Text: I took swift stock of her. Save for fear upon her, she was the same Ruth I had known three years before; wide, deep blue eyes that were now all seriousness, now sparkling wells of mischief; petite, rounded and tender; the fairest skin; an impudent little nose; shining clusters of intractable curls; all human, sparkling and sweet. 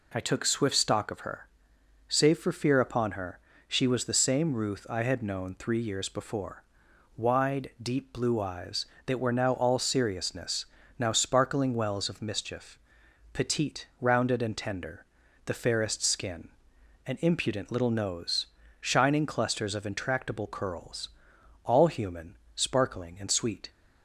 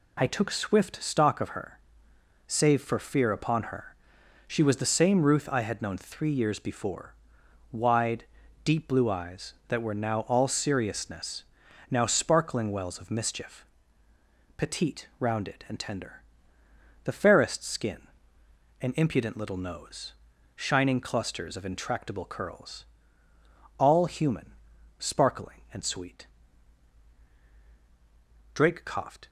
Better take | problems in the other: first | goes on to say "Drake coughed"; noticeable; from 28.5 s on; 0.74 s long

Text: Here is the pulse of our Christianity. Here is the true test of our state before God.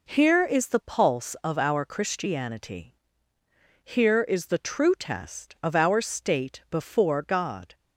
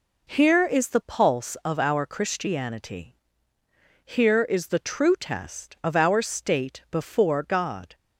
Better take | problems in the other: neither | none

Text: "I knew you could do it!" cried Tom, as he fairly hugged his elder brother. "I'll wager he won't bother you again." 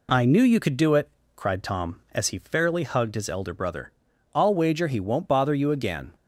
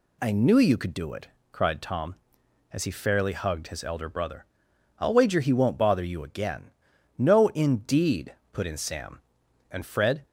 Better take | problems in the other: first | goes on to say "No indeed put in Sam and Fred"; strong; from 7.1 s on; 3.0 s long

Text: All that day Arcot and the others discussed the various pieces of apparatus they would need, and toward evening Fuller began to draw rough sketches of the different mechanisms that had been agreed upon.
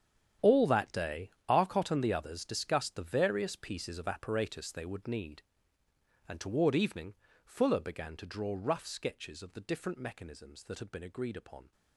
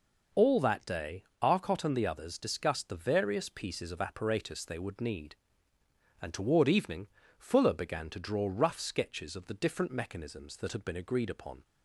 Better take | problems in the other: second | gets quieter; strong; throughout; 14.5 dB // pauses between "day" and "Arcot"; slight; at 1.3 s; 0.18 s long; slight in the second // pauses between "evening" and "Fuller"; slight; at 7.1 s; 0.28 s long; slight in the second

